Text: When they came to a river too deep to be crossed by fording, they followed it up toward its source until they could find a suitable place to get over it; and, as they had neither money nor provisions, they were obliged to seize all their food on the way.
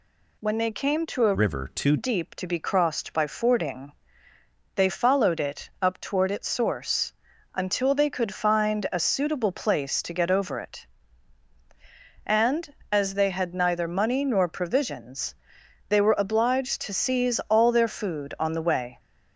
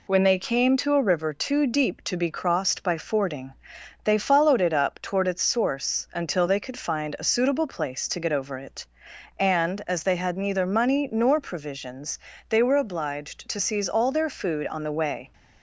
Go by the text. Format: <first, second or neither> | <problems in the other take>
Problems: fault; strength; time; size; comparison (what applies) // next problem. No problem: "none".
second | changes voice from "river" to "too"; from 1.3 to 1.9 s; 0.6 s long // pauses between "source" and "until"; at 7.1 s; 0.40 s long